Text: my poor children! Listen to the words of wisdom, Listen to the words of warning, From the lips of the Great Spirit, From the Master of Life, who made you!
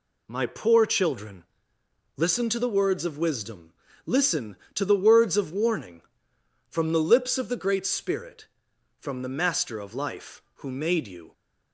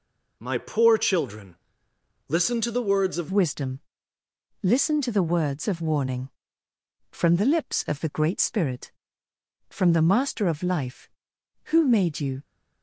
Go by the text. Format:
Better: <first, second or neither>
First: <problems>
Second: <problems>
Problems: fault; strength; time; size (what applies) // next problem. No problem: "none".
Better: first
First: none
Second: changes voice at "wisdom"; from 3.3 s on; 9.1 s long